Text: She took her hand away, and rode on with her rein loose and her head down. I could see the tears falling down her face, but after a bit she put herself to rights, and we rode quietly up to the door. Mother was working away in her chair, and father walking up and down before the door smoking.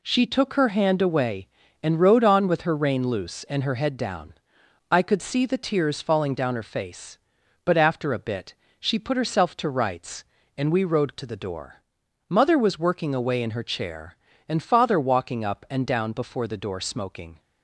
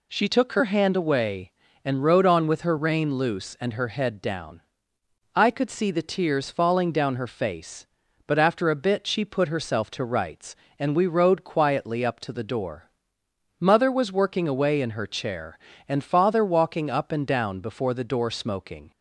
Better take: second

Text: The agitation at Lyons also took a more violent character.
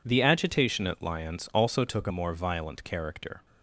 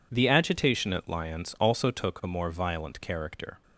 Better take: second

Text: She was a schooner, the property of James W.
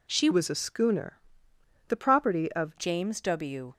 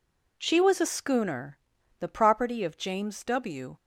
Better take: second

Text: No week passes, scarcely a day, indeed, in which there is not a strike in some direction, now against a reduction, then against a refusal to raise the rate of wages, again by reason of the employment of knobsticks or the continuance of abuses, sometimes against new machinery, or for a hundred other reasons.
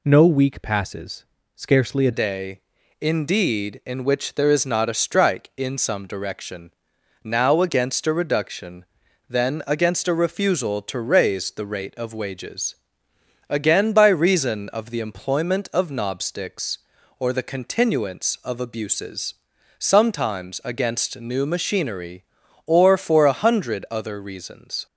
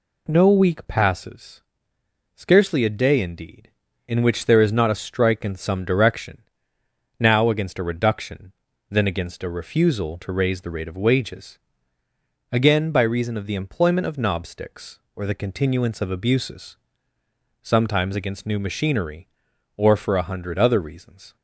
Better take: second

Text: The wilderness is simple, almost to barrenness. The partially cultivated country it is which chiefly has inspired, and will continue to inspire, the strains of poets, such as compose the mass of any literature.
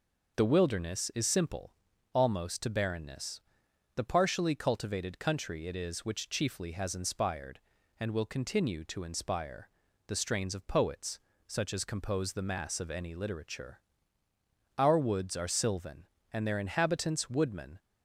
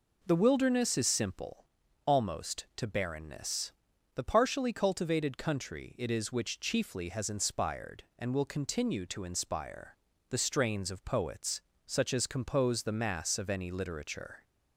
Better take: second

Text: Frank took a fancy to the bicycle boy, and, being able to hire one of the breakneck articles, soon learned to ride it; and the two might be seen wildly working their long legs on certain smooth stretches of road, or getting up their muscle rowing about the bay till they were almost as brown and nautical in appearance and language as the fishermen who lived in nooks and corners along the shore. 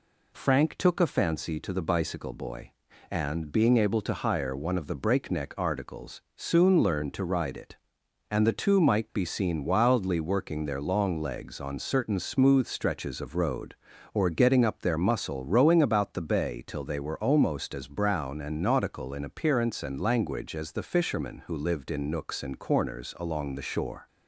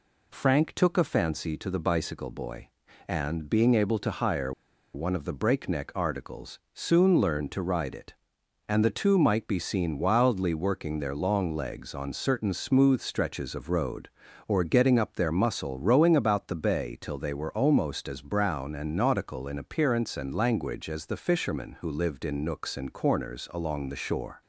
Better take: first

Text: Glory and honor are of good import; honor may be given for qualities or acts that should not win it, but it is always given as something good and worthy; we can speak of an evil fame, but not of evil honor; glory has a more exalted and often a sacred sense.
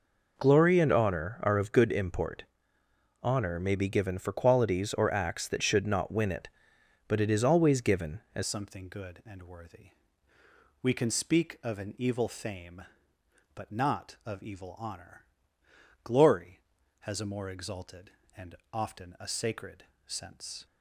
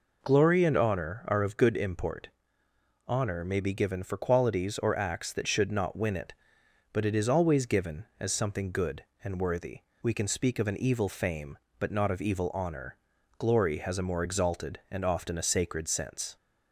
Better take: second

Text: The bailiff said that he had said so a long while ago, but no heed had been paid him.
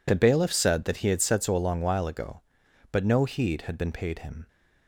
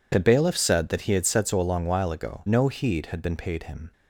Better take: first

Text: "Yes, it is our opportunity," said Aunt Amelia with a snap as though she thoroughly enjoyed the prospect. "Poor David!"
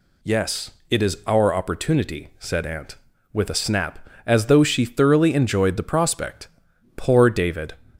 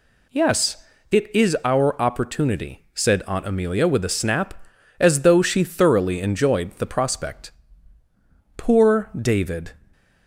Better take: second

